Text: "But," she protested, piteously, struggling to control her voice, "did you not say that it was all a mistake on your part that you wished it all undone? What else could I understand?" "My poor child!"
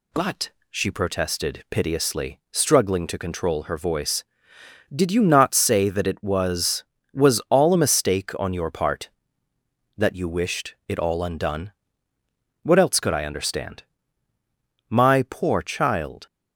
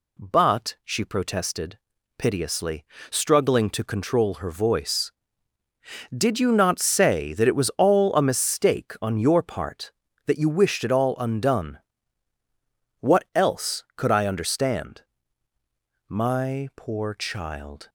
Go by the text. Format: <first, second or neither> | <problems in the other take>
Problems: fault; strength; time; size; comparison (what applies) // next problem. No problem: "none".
second | says "was" twice; at 7.1 s